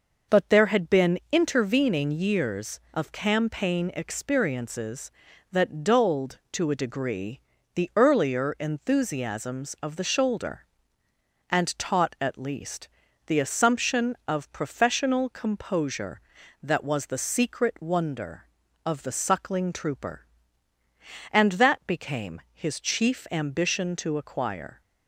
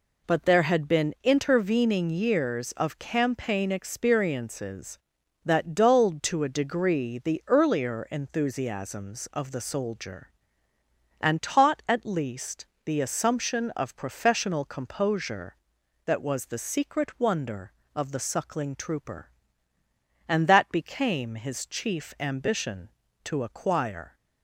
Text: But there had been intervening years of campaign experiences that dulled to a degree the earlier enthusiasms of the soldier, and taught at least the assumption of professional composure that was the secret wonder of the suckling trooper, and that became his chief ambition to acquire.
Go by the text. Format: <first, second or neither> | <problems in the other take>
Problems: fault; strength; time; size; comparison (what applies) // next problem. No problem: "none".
second | pauses between "degree" and "the"; slight; at 7.4 s; 0.34 s long // says "shoulder" for "soldier"; at 10.0 s // pauses between "least" and "the"; at 12.8 s; 0.38 s long; slight in the second